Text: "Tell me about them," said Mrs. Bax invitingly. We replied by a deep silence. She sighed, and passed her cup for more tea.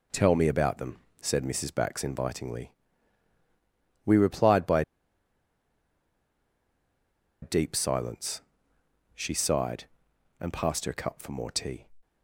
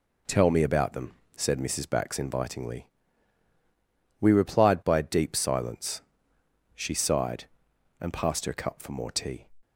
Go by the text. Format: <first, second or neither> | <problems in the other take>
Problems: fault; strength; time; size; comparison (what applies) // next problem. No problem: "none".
second | pauses between "by" and "a"; strong; at 4.8 s; 2.6 s long